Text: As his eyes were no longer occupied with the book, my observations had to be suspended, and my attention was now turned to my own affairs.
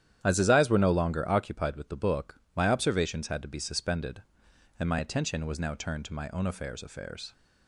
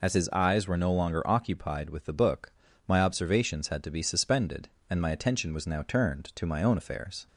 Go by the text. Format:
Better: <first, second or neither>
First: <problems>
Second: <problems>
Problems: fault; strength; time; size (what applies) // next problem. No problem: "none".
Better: second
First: starts louder than the rest; strong; until 1.2 s; 10.5 dB // says "affairs" twice; at 6.8 s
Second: none